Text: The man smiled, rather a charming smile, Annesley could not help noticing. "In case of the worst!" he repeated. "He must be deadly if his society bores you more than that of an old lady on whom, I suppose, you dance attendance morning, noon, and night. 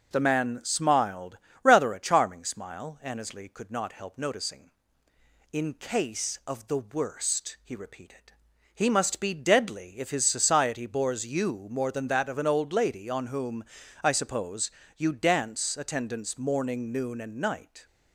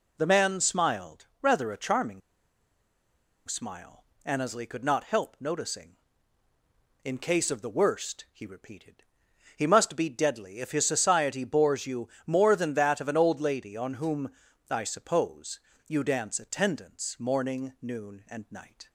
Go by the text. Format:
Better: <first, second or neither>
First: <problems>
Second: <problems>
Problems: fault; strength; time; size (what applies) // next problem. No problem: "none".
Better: first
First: none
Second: pauses between "charming" and "smile"; strong; at 2.2 s; 1.2 s long // pauses between "you" and "more"; slight; at 12.0 s; 0.18 s long